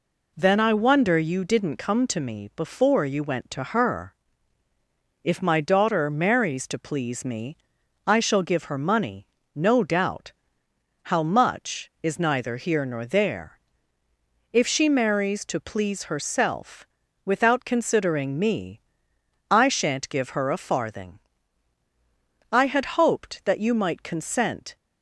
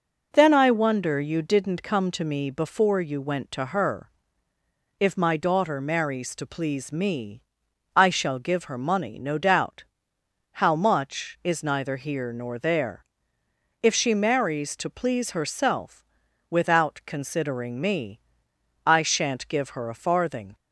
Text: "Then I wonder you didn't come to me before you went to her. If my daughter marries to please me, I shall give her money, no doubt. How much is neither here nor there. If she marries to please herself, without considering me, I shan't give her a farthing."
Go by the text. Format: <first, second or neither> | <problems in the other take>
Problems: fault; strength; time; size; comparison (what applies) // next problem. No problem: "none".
second | goes on to say "I had hoped that you might consent"; strong; from 22.5 s on; 2.2 s long